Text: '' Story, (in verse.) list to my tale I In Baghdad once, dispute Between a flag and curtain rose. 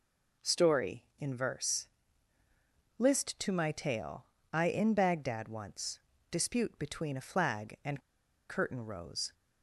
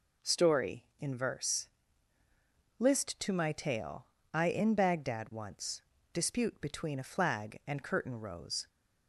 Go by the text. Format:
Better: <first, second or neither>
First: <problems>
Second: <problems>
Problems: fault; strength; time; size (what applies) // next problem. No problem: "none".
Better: second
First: pauses between "tale" and "I"; slight; at 4.2 s; 0.28 s long // pauses between "and" and "curtain"; noticeable; at 7.9 s; 0.49 s long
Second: pauses between "tale" and "I"; slight; at 4.0 s; 0.28 s long